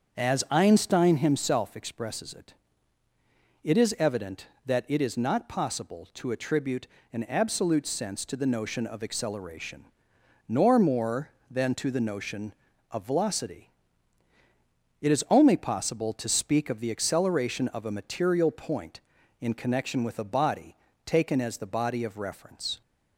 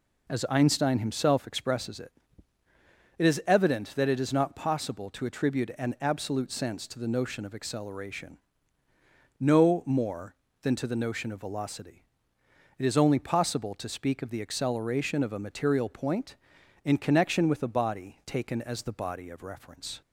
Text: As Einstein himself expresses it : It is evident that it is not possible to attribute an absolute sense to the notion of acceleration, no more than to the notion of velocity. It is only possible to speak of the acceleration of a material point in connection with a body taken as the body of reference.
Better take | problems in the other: second | starts louder than the rest; until 1.2 s; 7 dB // pauses between "attribute" and "an"; slight; at 6.8 s; 0.24 s long // says "nor" for "no"; at 10.4 s // pauses between "body" and "taken"; slight; at 20.7 s; 0.30 s long

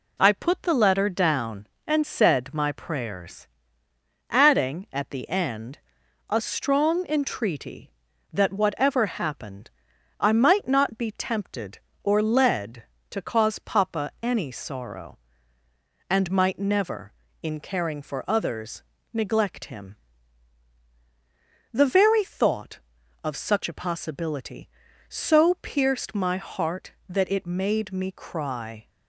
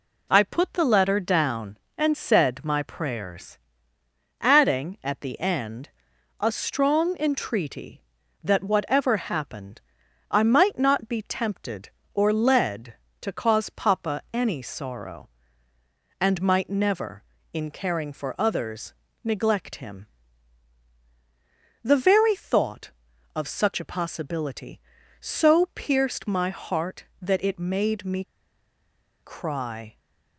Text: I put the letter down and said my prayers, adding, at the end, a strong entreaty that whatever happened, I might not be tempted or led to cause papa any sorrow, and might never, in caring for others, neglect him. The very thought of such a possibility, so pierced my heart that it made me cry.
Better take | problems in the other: first | pauses between "me" and "cry"; at 28.2 s; 0.98 s long

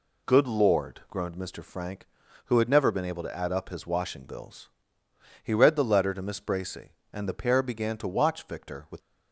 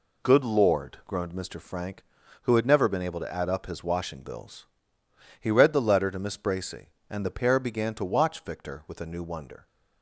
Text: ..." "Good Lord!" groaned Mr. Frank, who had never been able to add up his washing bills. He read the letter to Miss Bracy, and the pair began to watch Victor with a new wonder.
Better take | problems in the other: second | stops before "a new wonder"; at 8.9 s

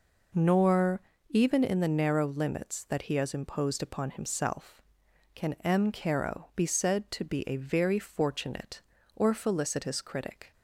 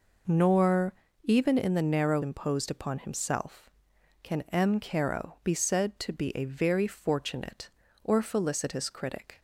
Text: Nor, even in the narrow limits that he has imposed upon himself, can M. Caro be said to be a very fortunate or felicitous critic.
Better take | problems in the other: first | skips "limits that he has"; at 2.2 s

